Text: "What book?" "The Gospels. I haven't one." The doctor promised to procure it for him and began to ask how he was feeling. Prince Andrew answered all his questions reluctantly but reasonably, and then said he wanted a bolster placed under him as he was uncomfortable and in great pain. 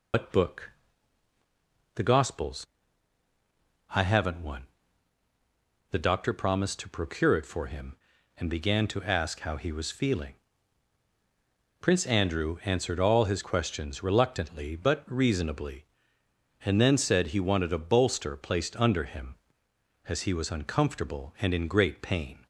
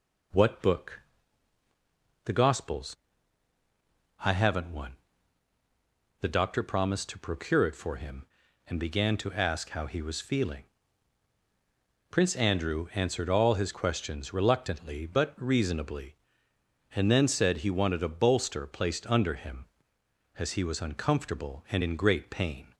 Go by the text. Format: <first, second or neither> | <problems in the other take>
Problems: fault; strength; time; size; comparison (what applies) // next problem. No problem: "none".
second | loses the start of "What"; at 0.1 s; 115 ms